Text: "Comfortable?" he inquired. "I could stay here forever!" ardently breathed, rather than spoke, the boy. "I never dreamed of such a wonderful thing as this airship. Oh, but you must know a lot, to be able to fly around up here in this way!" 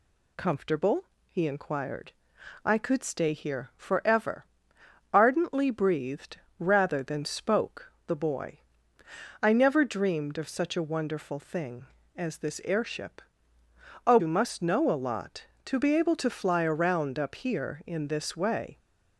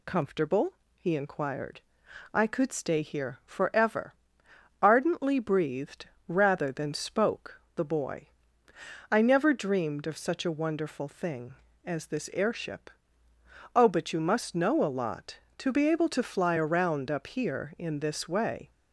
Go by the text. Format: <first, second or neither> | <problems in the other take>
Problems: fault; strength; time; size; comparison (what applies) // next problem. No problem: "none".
second | skips "but"; at 14.1 s